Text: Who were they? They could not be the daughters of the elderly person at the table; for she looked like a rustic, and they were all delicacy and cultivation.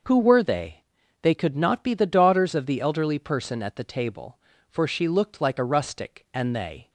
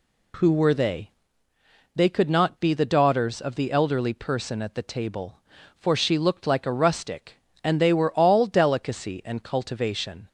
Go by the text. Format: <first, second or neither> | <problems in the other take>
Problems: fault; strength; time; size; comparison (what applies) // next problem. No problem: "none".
second | starts louder than the rest; noticeable; until 1.4 s; 6 dB // stops before "were all delicacy and cultivation"; at 6.8 s